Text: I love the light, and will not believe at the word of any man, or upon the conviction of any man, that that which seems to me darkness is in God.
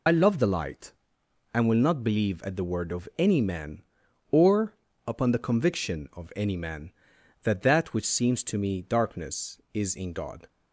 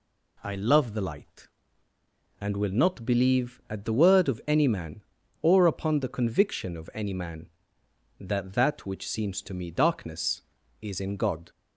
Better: second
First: loses the start of "I"; at 0.0 s; 40 ms // pauses between "or" and "upon"; slight; at 4.7 s; 0.34 s long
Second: none

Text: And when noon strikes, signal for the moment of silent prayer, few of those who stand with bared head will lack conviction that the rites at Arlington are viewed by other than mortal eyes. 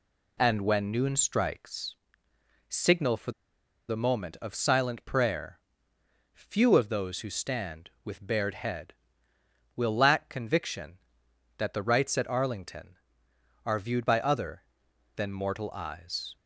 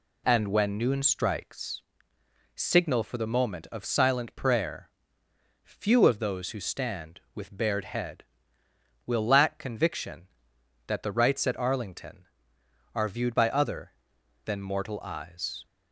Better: second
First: pauses between "for" and "the"; noticeable; at 3.3 s; 0.56 s long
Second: none

